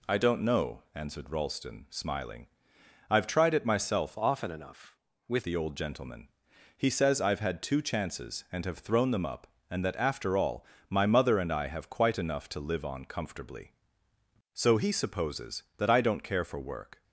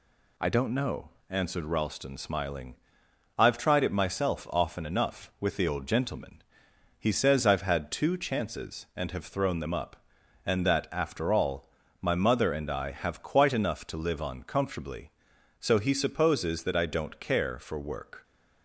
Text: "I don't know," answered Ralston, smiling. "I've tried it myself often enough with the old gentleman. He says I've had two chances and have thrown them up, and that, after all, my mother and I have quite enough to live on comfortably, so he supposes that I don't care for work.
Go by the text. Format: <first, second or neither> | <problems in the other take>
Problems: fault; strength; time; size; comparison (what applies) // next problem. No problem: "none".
second | changes voice from "often" to "with"; from 4.1 to 5.4 s; 1.3 s long